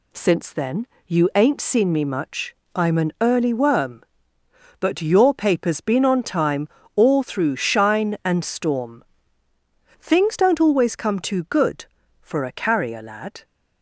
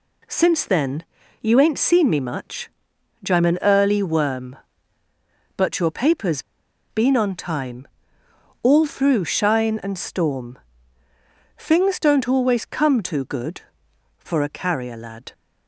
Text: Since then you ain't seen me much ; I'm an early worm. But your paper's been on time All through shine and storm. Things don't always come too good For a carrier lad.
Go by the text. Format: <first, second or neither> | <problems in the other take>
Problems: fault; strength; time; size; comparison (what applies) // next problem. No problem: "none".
first | pauses between "then" and "you"; at 1.0 s; 0.38 s long; slight in the first // pauses between "paper's" and "been"; noticeable; at 6.4 s; 0.49 s long // pauses between "time" and "All"; noticeable; at 7.8 s; 0.76 s long; slight in the first